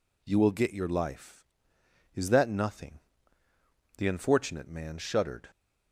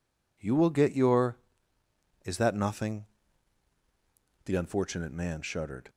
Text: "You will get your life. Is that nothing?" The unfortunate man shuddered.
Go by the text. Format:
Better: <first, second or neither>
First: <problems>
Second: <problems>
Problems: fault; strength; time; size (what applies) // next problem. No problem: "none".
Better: first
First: none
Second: skips "life"; at 1.8 s